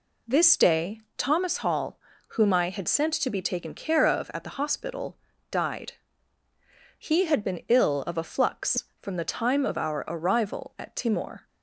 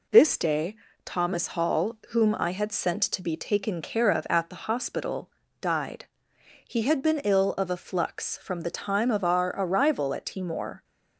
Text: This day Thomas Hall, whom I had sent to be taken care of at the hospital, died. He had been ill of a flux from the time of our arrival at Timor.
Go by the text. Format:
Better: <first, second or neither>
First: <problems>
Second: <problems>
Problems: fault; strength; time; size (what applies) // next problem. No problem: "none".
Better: neither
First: pauses between "day" and "Thomas"; slight; at 1.0 s; 0.18 s long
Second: pauses between "day" and "Thomas"; slight; at 0.7 s; 0.28 s long